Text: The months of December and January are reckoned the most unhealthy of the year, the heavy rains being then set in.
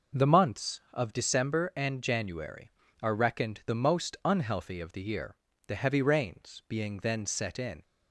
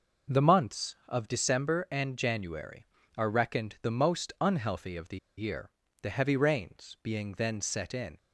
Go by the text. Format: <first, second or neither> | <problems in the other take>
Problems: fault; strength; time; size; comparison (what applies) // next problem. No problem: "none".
first | pauses between "the" and "year"; slight; at 5.1 s; 0.20 s long